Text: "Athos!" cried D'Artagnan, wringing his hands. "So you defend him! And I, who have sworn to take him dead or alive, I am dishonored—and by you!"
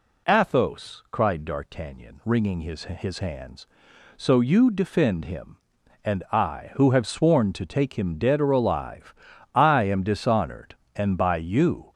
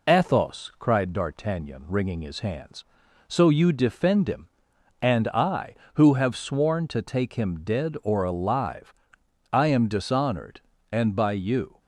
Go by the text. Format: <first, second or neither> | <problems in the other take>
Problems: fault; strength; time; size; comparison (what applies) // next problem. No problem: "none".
second | says "his" twice; at 2.8 s